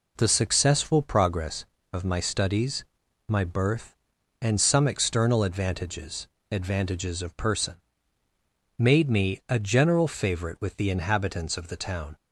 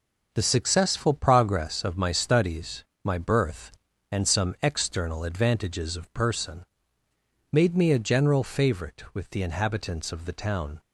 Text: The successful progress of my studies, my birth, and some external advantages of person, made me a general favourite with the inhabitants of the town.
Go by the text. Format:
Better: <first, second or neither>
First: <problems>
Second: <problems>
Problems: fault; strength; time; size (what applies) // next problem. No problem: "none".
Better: second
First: says "advantages" twice; at 6.4 s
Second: none